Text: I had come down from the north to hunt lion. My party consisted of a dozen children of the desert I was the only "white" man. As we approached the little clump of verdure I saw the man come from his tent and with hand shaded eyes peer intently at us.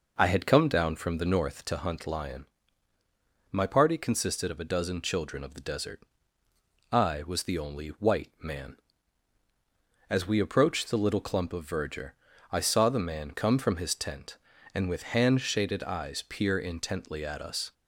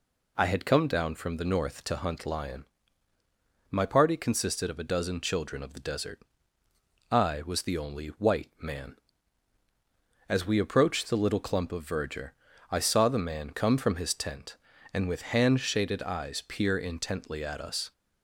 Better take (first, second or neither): second